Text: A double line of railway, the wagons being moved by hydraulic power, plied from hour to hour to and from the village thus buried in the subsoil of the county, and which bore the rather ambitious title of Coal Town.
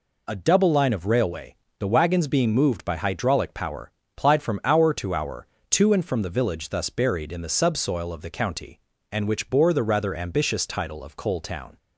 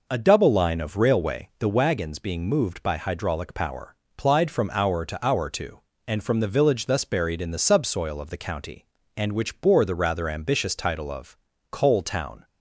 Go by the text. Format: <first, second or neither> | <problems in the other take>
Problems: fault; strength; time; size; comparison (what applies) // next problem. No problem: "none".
first | starts louder than the rest; noticeable; until 1.8 s; 5 dB // pauses between "of" and "Coal"; slight; at 11.3 s; 0.36 s long